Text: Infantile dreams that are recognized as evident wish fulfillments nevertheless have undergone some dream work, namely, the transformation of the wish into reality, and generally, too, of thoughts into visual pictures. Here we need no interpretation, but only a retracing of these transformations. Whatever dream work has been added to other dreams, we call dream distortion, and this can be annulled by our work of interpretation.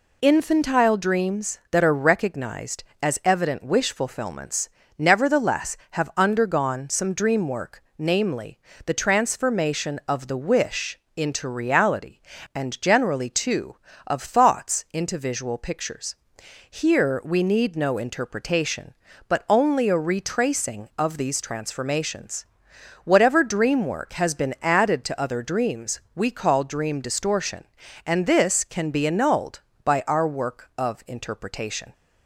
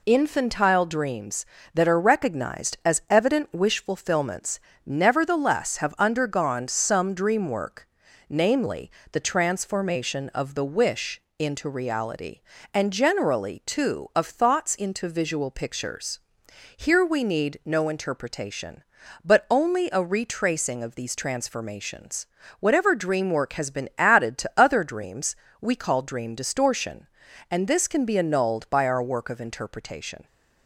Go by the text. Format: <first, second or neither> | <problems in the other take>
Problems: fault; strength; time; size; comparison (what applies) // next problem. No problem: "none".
neither | pauses between "fulfillments" and "nevertheless"; slight; the same in both // pauses between "wish" and "into"; slight; the same in both